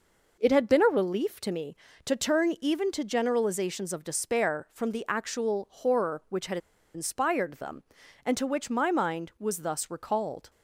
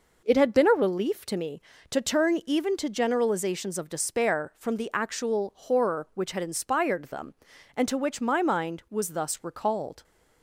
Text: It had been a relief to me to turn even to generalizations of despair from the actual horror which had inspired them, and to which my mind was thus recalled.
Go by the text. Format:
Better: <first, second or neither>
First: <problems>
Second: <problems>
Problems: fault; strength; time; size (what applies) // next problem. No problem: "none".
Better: second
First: pauses between "had" and "inspired"; at 6.5 s; 0.36 s long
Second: none